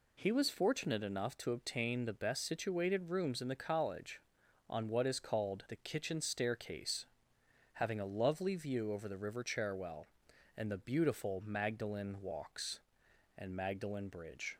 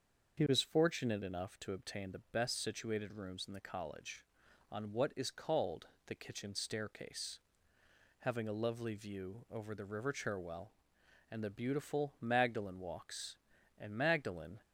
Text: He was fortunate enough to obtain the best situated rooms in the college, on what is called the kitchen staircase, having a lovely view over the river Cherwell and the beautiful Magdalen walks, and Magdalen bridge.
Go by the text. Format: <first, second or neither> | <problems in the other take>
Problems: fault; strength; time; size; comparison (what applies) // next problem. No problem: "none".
first | starts louder than the rest; until 1.4 s; 6.5 dB // pauses between "called" and "the"; slight; at 5.8 s; 0.18 s long // stops before "bridge"; at 14.6 s